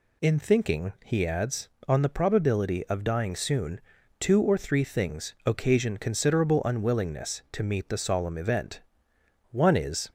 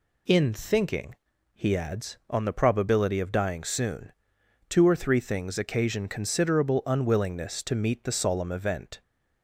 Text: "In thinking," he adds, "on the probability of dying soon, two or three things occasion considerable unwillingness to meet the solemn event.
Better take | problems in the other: second | goes on to say "One is"; from 9.5 s on; 0.60 s long

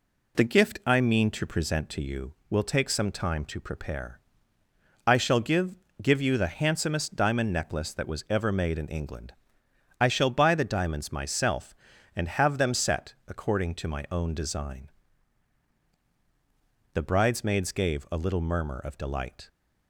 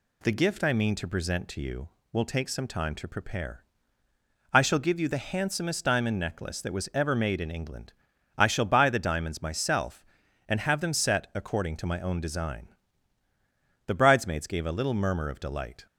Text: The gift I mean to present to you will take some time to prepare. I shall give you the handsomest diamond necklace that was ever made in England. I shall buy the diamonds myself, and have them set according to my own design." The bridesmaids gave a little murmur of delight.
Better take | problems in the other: second | says "give" twice; at 6.0 s

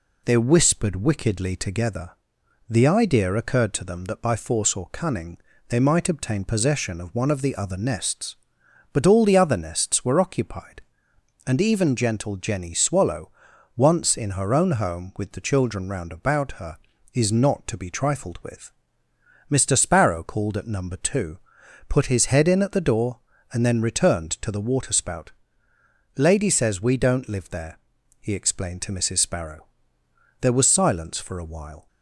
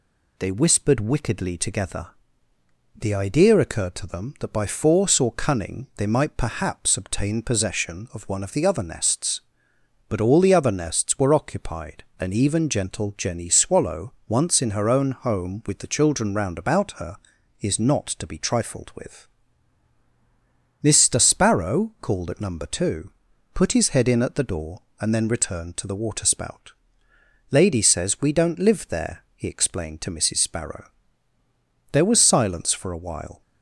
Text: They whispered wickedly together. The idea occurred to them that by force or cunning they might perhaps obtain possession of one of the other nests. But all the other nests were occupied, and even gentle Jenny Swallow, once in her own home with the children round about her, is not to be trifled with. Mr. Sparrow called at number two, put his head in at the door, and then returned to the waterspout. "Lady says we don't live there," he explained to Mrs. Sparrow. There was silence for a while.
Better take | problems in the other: second | pauses between "cunning" and "they"; slight; at 5.3 s; 0.30 s long // skips "perhaps"; at 6.0 s

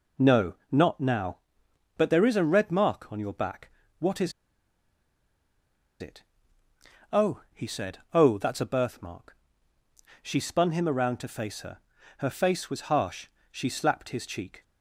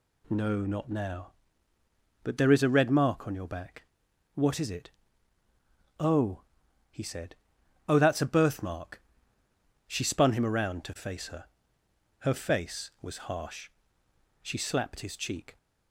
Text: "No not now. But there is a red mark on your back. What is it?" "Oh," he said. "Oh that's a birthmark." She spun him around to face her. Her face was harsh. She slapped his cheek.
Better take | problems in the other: second | pauses between "No" and "not"; slight; at 0.5 s; 0.16 s long // pauses between "is" and "it"; strong; at 4.3 s; 1.6 s long

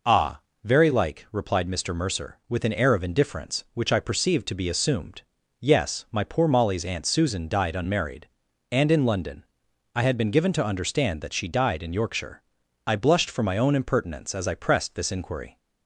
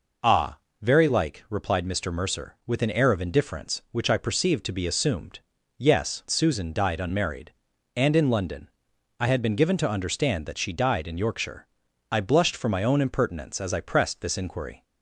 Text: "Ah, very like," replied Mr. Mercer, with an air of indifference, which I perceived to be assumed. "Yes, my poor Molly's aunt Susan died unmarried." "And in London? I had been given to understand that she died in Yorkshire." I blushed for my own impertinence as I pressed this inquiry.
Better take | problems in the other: first | skips "my poor Molly's aunt"; at 6.2 s

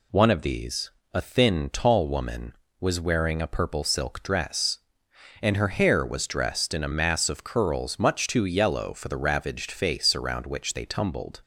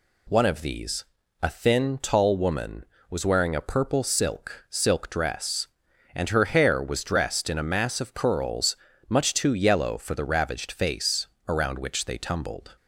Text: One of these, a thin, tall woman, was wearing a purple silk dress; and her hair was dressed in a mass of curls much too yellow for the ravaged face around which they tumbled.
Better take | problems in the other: first | says "silk" twice; at 4.6 s // pauses between "curls" and "much"; slight; at 8.7 s; 0.32 s long // pauses between "face" and "around"; slight; at 11.2 s; 0.18 s long

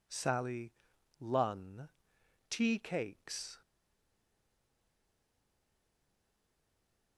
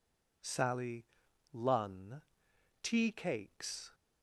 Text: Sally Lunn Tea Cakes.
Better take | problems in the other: second | pauses between "Sally" and "Lunn"; noticeable; at 0.7 s; 0.46 s long; noticeable in the second // pauses between "Lunn" and "Tea"; noticeable; at 1.8 s; 0.62 s long; noticeable in the second // stays silent after the last word; strong; from 3.6 s on; 3.5 s long

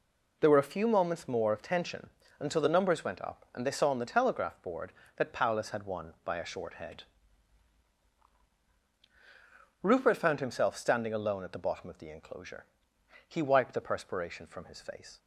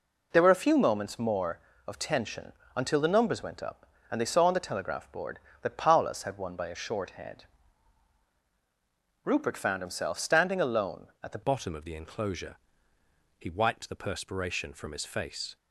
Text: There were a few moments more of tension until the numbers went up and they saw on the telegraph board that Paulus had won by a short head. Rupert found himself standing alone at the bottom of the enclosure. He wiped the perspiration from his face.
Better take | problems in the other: first | pauses between "tension" and "until"; slight; at 2.5 s; 0.22 s long; slight in the first // changes voice at "bottom"; from 11.4 s on; 4.1 s long

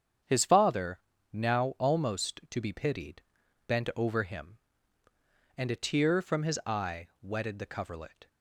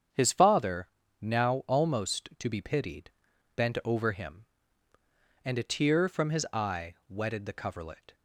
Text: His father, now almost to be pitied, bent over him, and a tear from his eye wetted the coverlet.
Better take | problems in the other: neither | starts louder than the rest; strong; the same in both

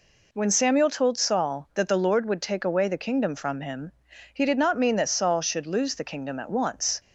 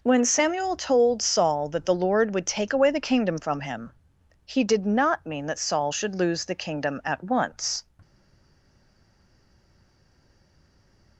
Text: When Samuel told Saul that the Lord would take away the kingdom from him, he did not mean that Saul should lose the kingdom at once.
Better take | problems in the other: first | stays silent after the last word; strong; from 8.0 s on; 3.1 s long

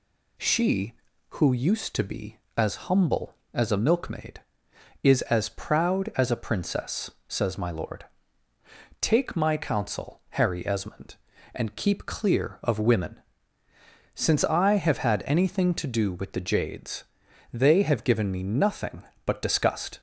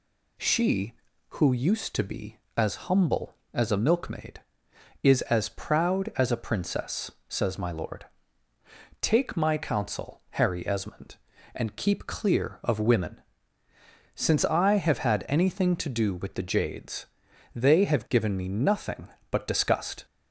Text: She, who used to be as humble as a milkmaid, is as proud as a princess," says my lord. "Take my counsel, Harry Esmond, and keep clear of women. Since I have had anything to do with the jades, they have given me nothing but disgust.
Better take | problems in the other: neither | none

